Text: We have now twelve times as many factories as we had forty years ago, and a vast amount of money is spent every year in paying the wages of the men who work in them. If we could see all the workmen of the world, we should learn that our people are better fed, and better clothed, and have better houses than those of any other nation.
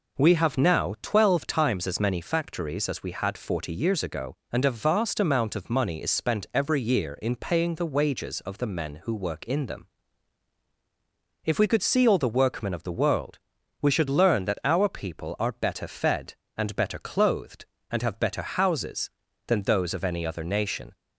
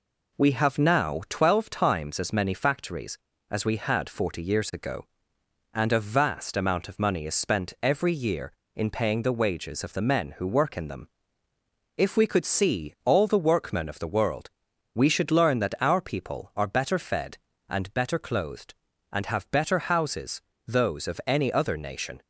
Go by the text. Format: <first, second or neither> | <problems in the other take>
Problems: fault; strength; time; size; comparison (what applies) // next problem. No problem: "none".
first | skips "than"; at 20.5 s